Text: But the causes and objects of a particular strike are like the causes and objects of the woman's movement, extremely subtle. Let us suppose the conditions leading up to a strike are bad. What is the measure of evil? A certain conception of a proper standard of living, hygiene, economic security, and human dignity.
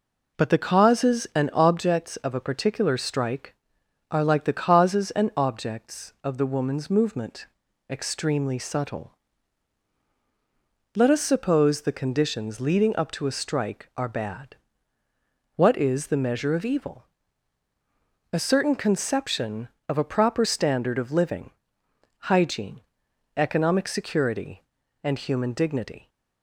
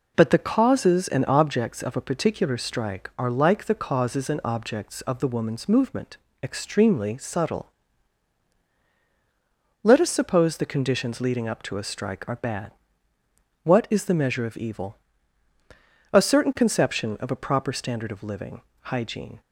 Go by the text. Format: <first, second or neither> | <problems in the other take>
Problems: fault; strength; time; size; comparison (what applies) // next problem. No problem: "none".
first | stops before "economic security and human dignity"; at 19.4 s